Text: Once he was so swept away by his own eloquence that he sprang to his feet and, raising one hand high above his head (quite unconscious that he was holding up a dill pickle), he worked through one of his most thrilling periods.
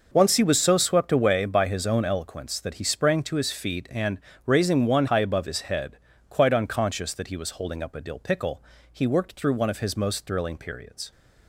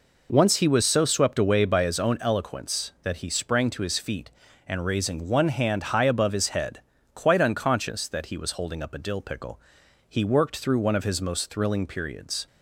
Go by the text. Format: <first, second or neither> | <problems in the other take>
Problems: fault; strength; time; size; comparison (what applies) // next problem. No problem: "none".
second | skips "hand"; at 5.0 s